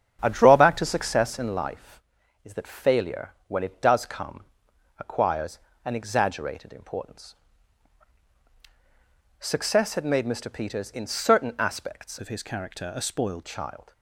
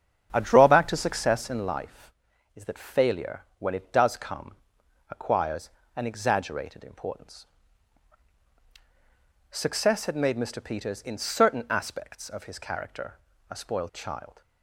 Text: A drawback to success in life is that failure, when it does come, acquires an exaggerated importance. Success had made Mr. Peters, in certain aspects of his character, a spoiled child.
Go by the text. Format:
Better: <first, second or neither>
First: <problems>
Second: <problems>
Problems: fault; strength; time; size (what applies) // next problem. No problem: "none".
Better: second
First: starts louder than the rest; strong; until 1.2 s; 8 dB // pauses between "acquires" and "an"; slight; at 5.5 s; 0.28 s long // changes voice from "of" to "spoiled"; from 12.1 to 13.4 s; 1.3 s long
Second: starts louder than the rest; strong; until 1.3 s; 8 dB // pauses between "acquires" and "an"; slight; at 5.6 s; 0.28 s long